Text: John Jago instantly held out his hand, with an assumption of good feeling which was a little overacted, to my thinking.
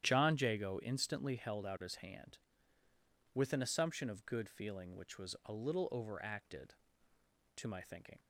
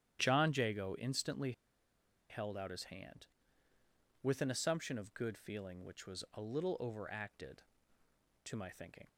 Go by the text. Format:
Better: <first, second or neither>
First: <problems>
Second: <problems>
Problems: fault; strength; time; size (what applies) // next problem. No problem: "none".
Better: first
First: starts louder than the rest; strong; until 1.1 s; 11 dB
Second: starts louder than the rest; strong; until 1.2 s; 11 dB // pauses between "instantly" and "held"; noticeable; at 1.5 s; 0.77 s long